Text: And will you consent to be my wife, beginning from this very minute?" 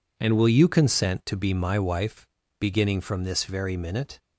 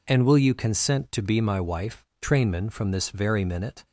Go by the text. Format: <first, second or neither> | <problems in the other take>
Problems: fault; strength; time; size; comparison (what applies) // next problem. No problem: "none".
first | says "trainman" for "beginning"; at 2.2 s